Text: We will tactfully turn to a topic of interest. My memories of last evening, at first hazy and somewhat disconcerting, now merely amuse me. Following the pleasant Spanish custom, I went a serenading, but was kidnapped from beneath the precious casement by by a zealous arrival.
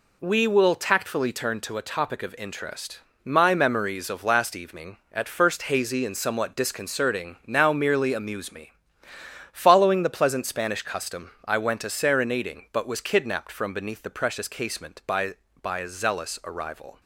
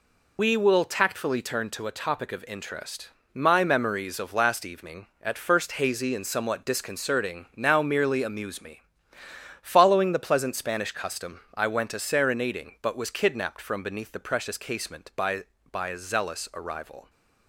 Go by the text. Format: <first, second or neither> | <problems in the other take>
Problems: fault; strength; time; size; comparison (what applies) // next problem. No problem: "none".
first | loses the start of "We"; at 0.3 s; 95 ms